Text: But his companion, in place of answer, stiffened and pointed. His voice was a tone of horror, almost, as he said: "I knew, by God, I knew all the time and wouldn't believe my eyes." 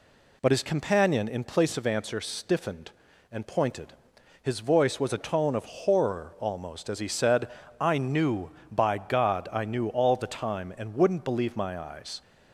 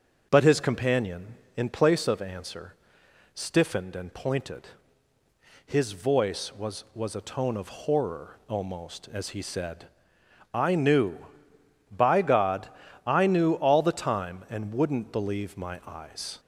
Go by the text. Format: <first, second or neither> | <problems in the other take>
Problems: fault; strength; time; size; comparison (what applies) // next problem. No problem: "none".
first | starts louder than the rest; noticeable; until 1.3 s; 6 dB // says "was" twice; at 6.9 s